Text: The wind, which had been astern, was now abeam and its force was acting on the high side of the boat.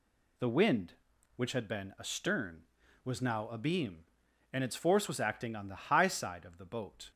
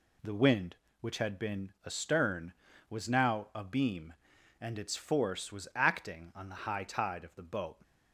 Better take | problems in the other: first | says "tide" for "side"; at 6.8 s

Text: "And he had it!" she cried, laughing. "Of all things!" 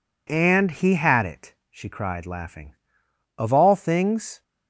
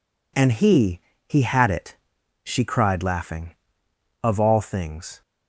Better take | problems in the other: first | says "he" twice; at 1.2 s

